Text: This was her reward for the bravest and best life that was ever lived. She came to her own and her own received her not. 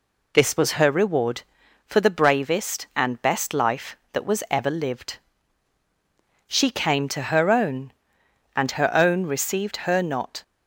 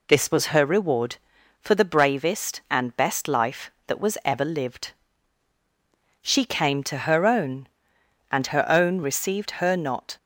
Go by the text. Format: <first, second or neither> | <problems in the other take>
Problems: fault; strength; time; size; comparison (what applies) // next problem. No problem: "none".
neither | none